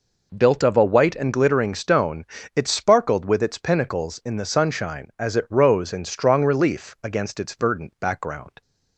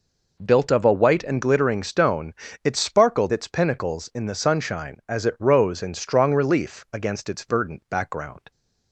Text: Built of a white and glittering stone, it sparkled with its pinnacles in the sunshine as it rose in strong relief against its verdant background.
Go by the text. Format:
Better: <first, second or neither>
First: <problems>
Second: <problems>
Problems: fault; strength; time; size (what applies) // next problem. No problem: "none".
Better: first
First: none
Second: skips "with"; at 3.3 s